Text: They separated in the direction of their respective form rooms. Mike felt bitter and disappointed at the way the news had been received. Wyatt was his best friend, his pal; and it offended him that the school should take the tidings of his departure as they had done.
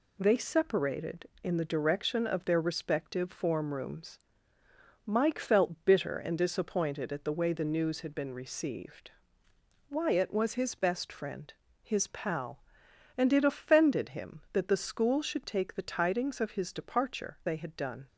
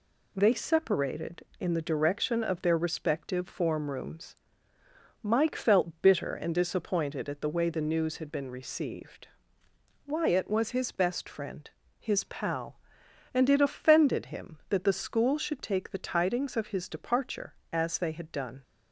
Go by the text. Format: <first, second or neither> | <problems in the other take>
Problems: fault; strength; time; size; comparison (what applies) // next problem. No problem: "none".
second | skips "as"; at 17.4 s